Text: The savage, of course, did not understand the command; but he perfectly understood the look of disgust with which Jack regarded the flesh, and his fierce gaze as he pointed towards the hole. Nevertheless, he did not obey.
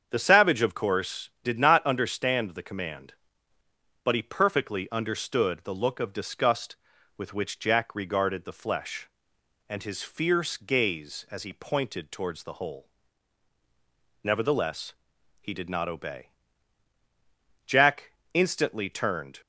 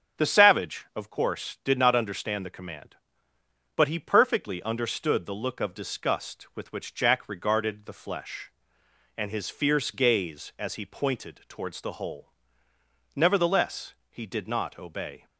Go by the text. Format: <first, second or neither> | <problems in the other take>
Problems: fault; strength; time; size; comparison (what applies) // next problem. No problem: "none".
second | starts louder than the rest; strong; until 1.1 s; 7.5 dB; also in the second // goes on to say "Jack instantly turned"; strong; from 17.6 s on; 1.7 s long